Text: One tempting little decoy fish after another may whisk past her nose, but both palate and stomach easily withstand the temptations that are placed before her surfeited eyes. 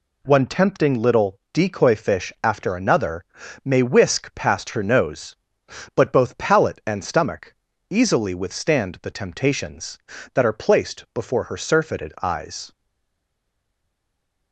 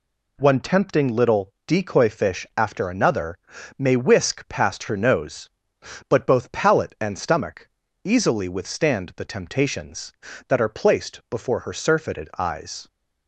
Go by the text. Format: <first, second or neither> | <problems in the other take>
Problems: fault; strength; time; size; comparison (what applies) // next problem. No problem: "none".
second | pauses between "another" and "may"; at 3.2 s; 0.40 s long; also in the second // pauses between "stomach" and "easily"; slight; at 7.5 s; 0.36 s long; slight in the second // stays silent after the last word; noticeable; from 12.7 s on; 1.8 s long